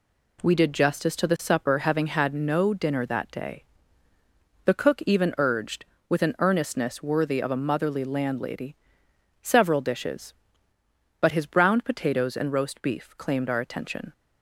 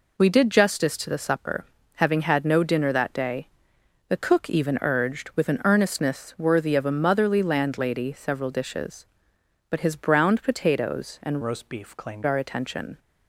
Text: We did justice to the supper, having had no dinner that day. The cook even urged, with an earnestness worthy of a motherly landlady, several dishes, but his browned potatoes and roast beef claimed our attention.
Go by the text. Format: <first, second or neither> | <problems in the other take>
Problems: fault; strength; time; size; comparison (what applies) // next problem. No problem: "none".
first | changes voice from "roast" to "claimed"; from 11.4 to 12.2 s; 0.8 s long